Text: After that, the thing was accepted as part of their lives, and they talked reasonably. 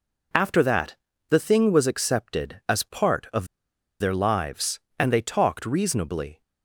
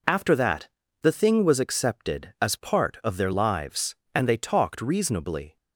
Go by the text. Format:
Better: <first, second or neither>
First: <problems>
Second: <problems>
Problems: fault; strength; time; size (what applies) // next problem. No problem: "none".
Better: second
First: pauses between "of" and "their"; noticeable; at 3.4 s; 0.53 s long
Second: none